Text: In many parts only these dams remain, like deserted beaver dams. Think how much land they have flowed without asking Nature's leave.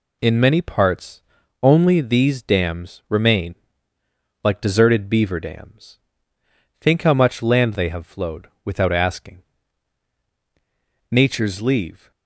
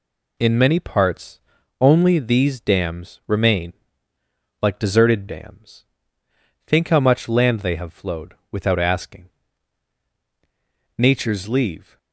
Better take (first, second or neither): first